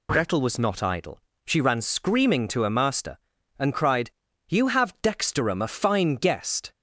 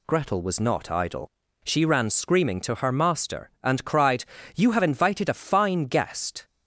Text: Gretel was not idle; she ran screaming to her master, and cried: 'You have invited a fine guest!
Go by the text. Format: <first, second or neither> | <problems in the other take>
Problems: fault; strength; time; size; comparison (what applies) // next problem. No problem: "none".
second | says "dexterum" for "invited"; at 5.0 s